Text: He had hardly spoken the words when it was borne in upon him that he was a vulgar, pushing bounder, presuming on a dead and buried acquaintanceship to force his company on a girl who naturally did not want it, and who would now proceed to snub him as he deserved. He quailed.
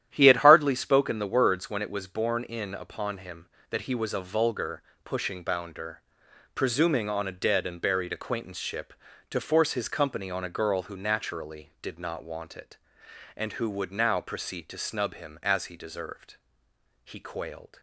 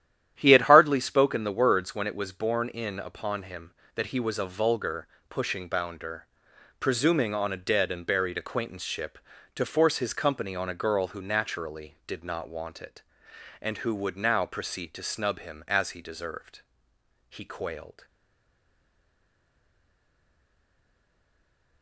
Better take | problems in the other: first | starts louder than the rest; strong; until 1.3 s; 11 dB; strong in the first // stays silent after the last word; strong; from 18.0 s on; 3.8 s long

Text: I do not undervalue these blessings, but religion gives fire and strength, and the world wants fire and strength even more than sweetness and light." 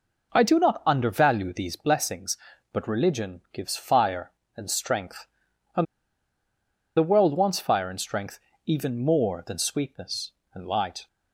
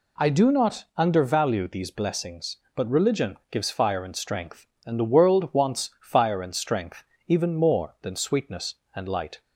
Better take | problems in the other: second | pauses between "and" and "the"; at 5.8 s; 1.1 s long // pauses between "strength" and "even"; slight; at 8.3 s; 0.28 s long; slight in the second

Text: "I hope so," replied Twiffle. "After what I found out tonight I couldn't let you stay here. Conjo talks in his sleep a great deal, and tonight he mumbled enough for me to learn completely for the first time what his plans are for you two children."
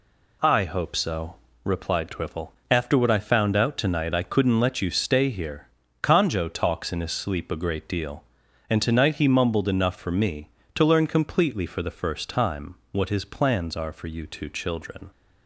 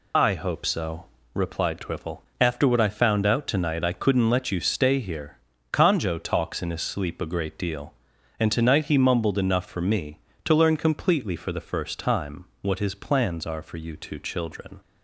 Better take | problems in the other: first | loses the start of "I"; at 0.1 s; 40 ms // pauses between "time" and "what"; slight; at 12.4 s; 0.18 s long; slight in the first

